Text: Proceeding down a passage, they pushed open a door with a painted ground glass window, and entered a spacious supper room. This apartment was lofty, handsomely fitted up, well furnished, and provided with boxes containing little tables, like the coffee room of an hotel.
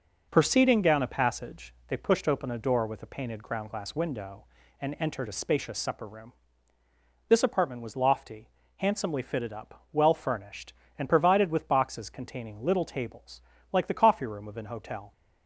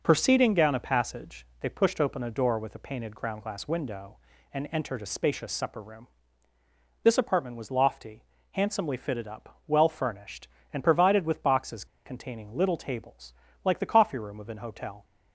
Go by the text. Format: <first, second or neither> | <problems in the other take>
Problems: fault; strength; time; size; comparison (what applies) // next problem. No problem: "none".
first | pauses between "boxes" and "containing"; slight; at 11.8 s; 0.20 s long